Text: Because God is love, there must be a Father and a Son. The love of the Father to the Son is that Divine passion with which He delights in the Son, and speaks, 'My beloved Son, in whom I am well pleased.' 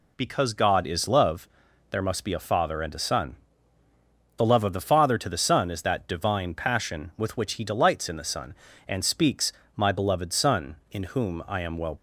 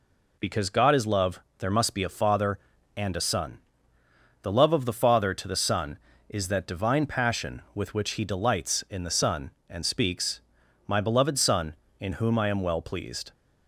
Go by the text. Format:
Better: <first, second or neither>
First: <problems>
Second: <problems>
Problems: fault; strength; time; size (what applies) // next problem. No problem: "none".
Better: second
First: stops before "pleased"; at 11.9 s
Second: none